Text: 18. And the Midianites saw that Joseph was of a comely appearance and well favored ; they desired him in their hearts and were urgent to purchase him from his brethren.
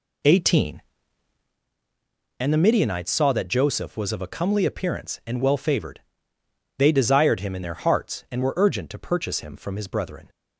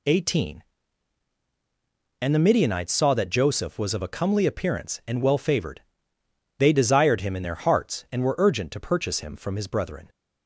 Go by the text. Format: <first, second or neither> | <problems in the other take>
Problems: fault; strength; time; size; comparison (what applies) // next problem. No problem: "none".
second | starts louder than the rest; slight; until 1.6 s; 2.5 dB